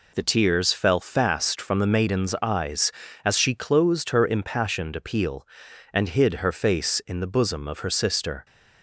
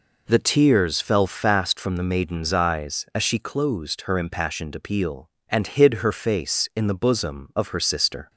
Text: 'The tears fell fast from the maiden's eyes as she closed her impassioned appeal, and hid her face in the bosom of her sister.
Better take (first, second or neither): neither